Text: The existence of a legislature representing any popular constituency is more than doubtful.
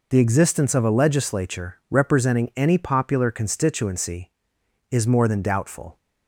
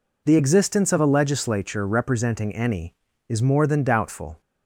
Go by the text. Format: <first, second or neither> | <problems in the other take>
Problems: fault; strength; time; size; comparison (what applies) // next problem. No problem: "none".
first | skips "popular constituency"; at 3.0 s